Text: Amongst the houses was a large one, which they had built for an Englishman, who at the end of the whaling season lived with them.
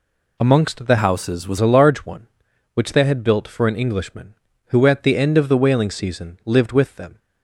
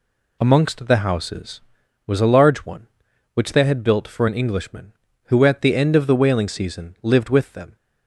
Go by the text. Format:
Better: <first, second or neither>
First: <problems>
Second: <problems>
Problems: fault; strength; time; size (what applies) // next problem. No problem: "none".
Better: second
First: changes voice from "houses" to "was"; from 0.9 to 1.5 s; 0.6 s long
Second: none